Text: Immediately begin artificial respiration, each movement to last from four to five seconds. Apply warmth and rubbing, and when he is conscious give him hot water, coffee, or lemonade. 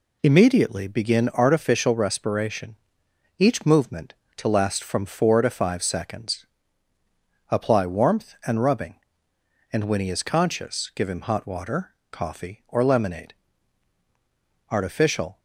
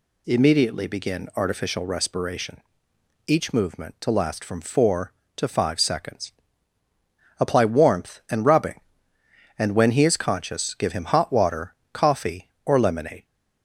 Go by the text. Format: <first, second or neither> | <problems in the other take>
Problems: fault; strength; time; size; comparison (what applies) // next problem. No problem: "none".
second | goes on to say "Artificial"; noticeable; from 14.6 s on; 0.70 s long